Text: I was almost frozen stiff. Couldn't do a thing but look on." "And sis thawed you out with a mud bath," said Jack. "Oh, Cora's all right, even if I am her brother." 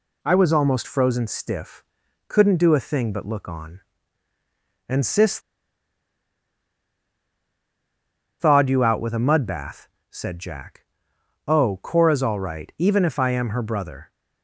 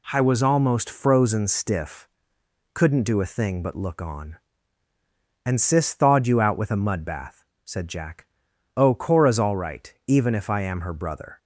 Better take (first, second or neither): second